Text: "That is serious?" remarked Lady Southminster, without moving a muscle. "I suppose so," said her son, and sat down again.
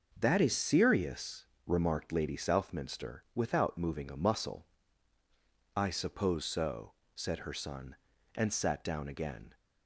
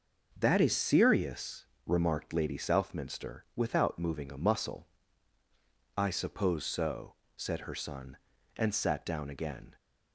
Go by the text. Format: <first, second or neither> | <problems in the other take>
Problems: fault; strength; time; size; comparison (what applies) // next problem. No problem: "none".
neither | none